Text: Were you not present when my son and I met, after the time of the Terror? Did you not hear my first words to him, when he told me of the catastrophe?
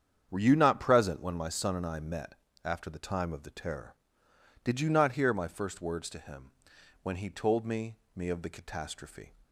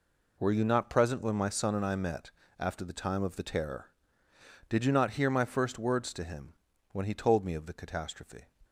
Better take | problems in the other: second | starts louder than the rest; strong; until 1.3 s; 8 dB // says "me" twice; at 8.1 s

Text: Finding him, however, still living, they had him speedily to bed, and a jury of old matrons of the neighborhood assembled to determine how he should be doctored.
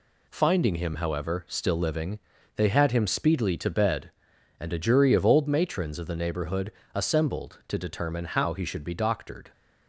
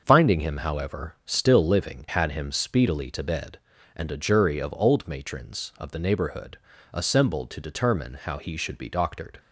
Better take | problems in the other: first | starts louder than the rest; until 1.0 s; 6 dB // skips "they"; at 2.0 s // pauses between "neighborhood" and "assembled"; slight; at 6.5 s; 0.36 s long; slight in the first

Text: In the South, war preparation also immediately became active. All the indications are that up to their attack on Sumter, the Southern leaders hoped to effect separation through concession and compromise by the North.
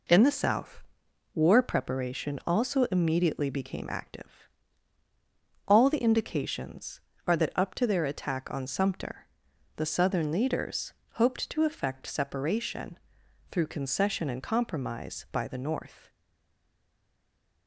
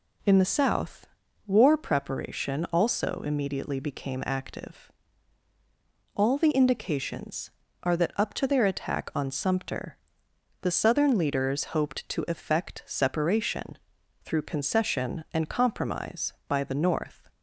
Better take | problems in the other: second | pauses between "leaders" and "hoped"; slight; at 10.9 s; 0.20 s long // pauses between "separation" and "through"; noticeable; at 12.9 s; 0.54 s long; also in the second // stays silent after the last word; noticeable; from 16.0 s on; 1.6 s long

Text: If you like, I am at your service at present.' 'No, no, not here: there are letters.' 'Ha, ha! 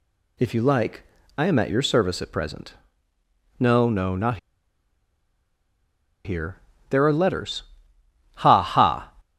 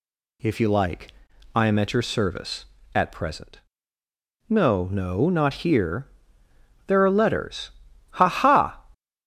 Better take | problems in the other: second | pauses between "not" and "here"; strong; at 4.3 s; 1.8 s long

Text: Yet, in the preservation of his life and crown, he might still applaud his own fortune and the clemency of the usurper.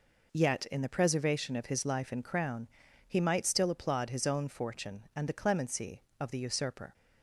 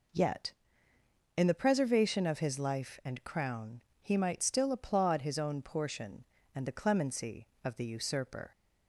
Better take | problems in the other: first | says "portion" for "fortune"; at 5.6 s

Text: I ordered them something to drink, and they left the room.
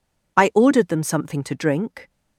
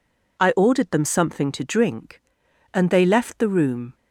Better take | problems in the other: second | stops before "and they left the room"; at 2.0 s

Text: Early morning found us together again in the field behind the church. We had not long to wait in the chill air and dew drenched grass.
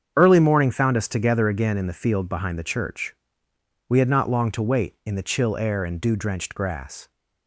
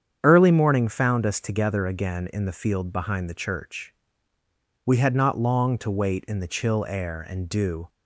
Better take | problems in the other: first | starts louder than the rest; strong; until 1.2 s; 8 dB; strong in the first // stops before "drenched grass"; at 7.8 s

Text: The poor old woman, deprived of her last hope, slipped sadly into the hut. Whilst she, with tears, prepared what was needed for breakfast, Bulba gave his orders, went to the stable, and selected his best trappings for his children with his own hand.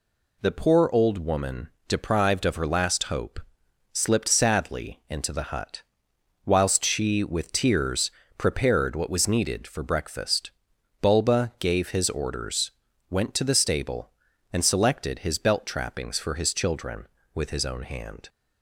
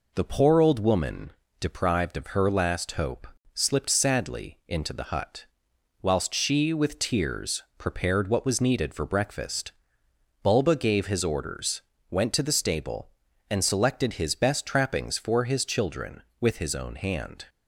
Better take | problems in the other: second | says "belt" for "best"; at 15.3 s

